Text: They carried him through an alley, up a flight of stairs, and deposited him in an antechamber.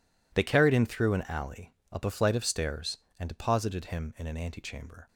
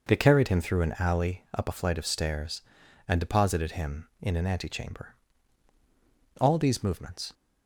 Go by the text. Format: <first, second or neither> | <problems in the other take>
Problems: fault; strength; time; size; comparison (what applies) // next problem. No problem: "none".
first | goes on to say "All these movements"; noticeable; from 6.3 s on; 0.94 s long